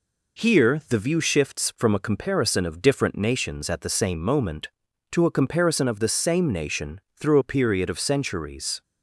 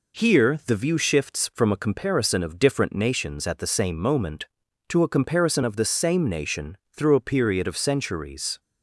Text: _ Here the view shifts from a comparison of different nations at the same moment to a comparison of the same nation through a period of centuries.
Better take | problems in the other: neither | pauses between "nation" and "through"; slight; the same in both

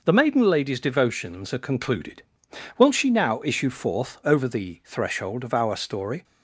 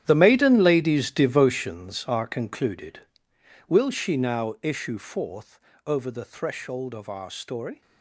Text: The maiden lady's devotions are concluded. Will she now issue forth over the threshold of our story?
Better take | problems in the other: first | gets quieter; strong; throughout; 14 dB // pauses between "forth" and "over"; slight; at 5.5 s; 0.28 s long

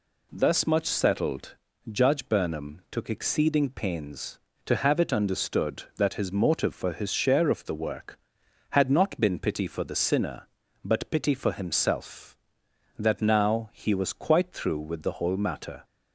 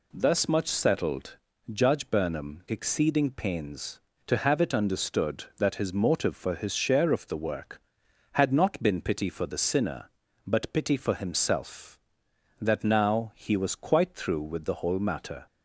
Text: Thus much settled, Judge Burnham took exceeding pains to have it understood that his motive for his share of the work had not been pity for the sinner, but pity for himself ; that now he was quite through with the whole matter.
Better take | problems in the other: first | skips "took"; at 2.6 s

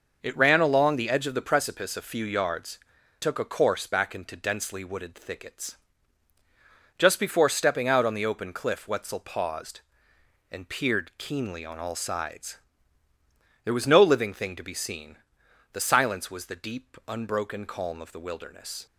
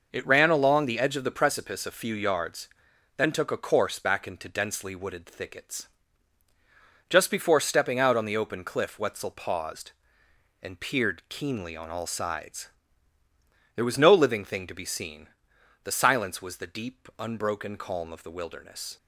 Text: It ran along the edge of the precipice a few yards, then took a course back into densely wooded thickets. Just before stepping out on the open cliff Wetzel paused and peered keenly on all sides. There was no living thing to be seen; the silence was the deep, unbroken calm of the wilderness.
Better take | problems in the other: second | skips "then"; at 3.0 s

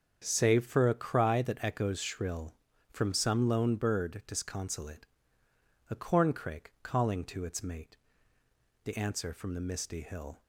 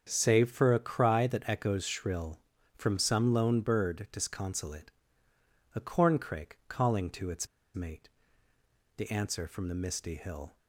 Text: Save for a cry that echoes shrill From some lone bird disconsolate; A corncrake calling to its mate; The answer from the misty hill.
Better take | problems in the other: first | starts louder than the rest; strong; until 1.1 s; 7 dB; strong in the first // pauses between "its" and "mate"; slight; at 7.4 s; 0.29 s long

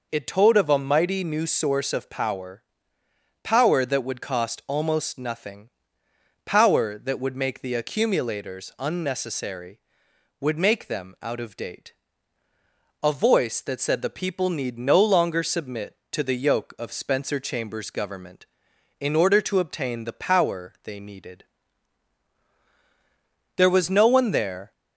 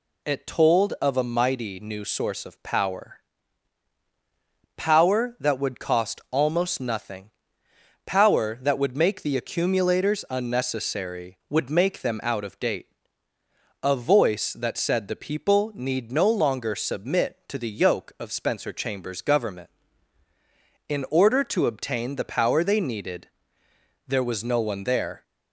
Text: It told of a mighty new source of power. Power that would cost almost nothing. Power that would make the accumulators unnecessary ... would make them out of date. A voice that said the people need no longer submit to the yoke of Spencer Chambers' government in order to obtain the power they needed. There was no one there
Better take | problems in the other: neither | none

